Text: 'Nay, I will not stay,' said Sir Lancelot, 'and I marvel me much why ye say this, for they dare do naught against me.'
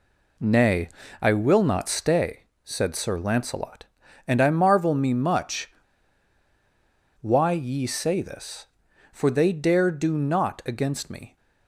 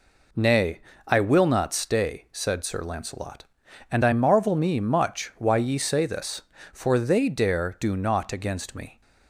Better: second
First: pauses between "much" and "why"; strong; at 5.7 s; 1.5 s long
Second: none

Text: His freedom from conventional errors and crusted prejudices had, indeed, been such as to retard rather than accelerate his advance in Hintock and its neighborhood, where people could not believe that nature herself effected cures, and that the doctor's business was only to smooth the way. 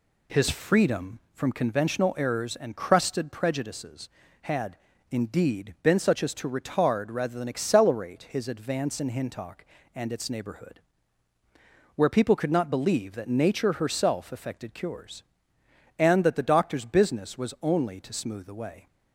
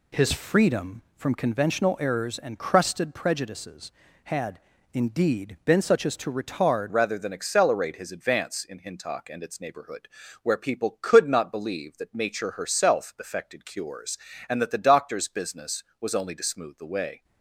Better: first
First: none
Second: changes voice at "rather"; from 6.8 s on; 10.4 s long

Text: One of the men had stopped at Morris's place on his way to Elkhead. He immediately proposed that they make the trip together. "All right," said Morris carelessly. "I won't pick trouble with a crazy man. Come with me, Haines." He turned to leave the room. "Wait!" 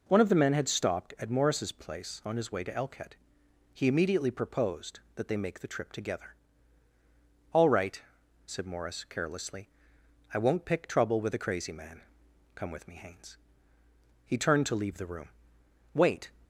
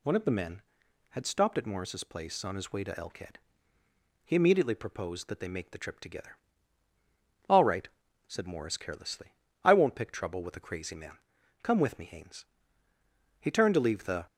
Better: first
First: none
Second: stops before "room Wait"; at 14.2 s

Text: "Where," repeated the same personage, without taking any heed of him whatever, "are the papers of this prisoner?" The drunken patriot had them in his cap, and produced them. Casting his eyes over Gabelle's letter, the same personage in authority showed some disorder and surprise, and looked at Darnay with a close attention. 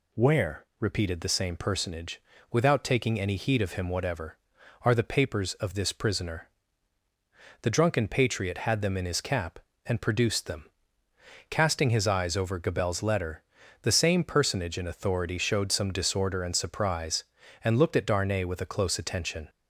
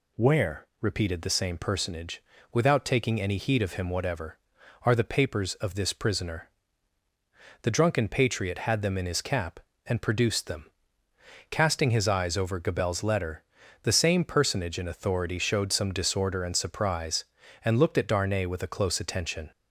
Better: neither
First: none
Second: none

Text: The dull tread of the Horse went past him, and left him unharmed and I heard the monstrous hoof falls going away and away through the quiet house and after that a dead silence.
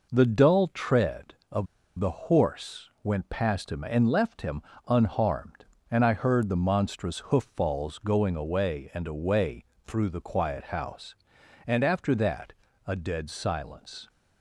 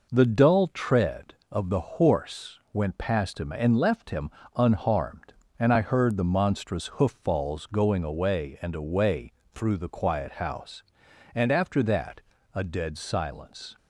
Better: second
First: pauses between "of" and "the"; slight; at 1.6 s; 0.32 s long // pauses between "him" and "unharmed"; slight; at 4.6 s; 0.24 s long // pauses between "away" and "through"; slight; at 9.6 s; 0.20 s long // pauses between "that" and "a"; slight; at 12.5 s; 0.34 s long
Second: pauses between "him" and "unharmed"; slight; at 4.3 s; 0.24 s long // pauses between "away" and "through"; slight; at 9.3 s; 0.20 s long // pauses between "that" and "a"; slight; at 12.2 s; 0.34 s long

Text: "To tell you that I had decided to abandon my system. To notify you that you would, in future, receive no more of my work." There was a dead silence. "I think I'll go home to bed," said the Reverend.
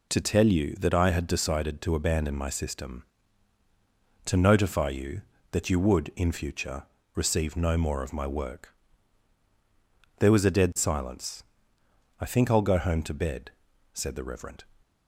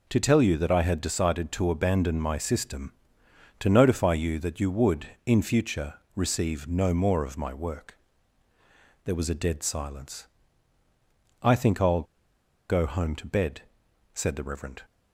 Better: first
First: none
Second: pauses between "I'll" and "go"; noticeable; at 12.0 s; 0.65 s long

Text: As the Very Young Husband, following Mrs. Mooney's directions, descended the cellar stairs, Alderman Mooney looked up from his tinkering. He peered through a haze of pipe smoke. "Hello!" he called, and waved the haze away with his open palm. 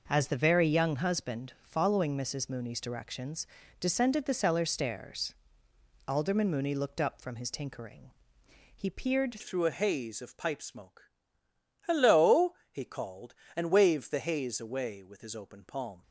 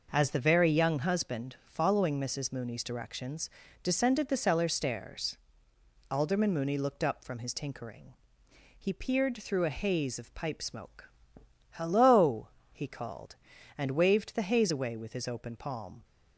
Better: second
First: changes voice at "through"; from 9.3 s on; 6.7 s long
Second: none

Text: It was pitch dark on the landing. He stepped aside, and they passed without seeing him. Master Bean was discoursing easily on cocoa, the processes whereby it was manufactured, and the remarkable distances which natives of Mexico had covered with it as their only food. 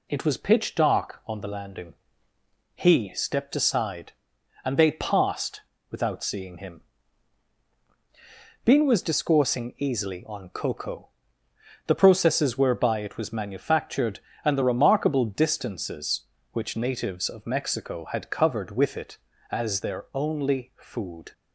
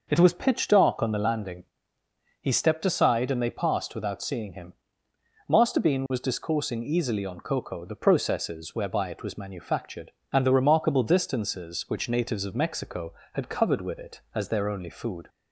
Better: second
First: pauses between "passed" and "without"; slight; at 5.6 s; 0.28 s long // skips "Master"; at 7.7 s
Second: none

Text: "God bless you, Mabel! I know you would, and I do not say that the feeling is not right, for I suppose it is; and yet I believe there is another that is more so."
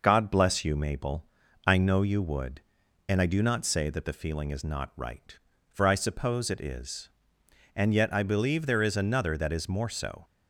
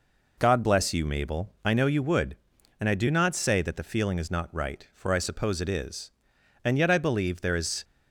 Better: first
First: none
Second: stops before "another that is more so"; at 7.8 s

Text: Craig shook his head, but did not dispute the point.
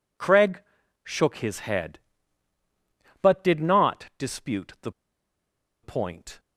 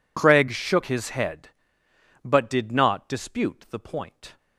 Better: second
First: pauses between "Craig" and "shook"; at 0.6 s; 0.42 s long // pauses between "the" and "point"; noticeable; at 4.9 s; 0.91 s long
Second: none

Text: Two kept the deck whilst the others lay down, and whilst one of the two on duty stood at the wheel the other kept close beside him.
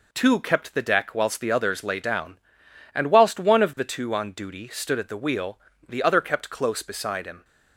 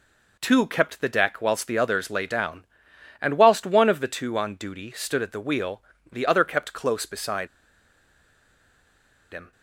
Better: first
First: pauses between "wheel" and "the"; slight; at 5.5 s; 0.30 s long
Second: pauses between "wheel" and "the"; slight; at 5.8 s; 0.30 s long // pauses between "beside" and "him"; strong; at 7.4 s; 1.8 s long

